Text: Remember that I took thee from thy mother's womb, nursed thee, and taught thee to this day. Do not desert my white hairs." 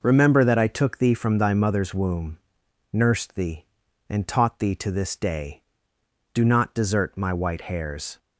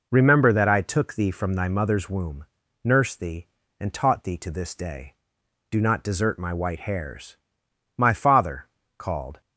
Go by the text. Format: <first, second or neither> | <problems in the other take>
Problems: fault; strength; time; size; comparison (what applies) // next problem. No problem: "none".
first | goes on to say "My father called"; from 7.9 s on; 1.4 s long